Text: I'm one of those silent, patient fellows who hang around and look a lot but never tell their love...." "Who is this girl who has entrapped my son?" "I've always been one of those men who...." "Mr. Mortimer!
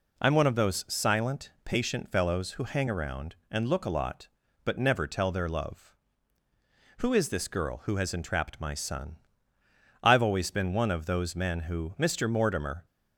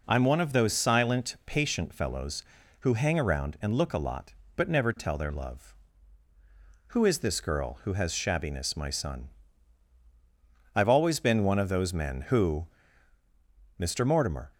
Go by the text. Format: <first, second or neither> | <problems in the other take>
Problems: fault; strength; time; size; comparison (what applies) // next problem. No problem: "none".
first | says "shabbiness" for "entrapped"; at 8.1 s